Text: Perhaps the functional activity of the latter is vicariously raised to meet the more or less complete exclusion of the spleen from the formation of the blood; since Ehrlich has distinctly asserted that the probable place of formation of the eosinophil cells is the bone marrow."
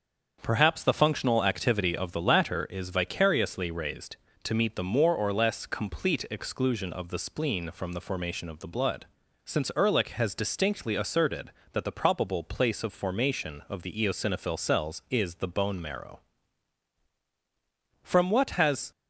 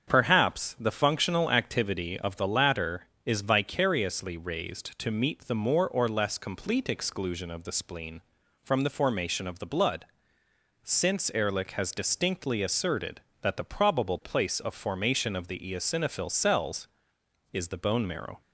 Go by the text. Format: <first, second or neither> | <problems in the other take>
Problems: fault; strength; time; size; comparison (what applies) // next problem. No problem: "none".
second | starts louder than the rest; until 1.4 s; 7 dB; strong in the second // goes on to say "From what has"; noticeable; from 18.0 s on; 0.88 s long